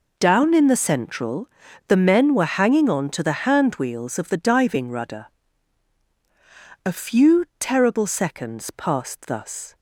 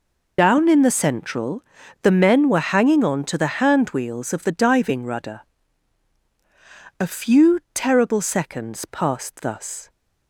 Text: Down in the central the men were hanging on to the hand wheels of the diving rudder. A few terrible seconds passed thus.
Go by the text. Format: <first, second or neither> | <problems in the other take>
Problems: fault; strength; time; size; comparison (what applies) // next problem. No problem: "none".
first | loses the start of "Down"; at 0.3 s; 50 ms // pauses between "central" and "the"; at 1.6 s; 0.40 s long; also in the first